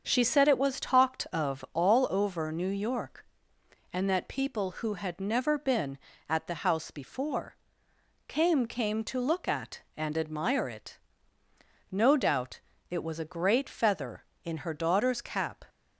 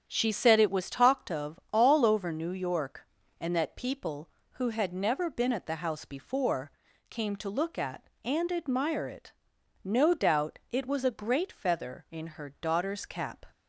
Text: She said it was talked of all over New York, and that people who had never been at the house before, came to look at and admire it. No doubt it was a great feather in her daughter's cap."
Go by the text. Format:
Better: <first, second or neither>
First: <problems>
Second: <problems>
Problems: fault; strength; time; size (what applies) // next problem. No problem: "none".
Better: second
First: starts louder than the rest; until 1.0 s; 7 dB // says "came" twice; at 8.6 s // pauses between "doubt" and "it"; slight; at 12.6 s; 0.30 s long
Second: starts louder than the rest; strong; until 1.0 s; 8.5 dB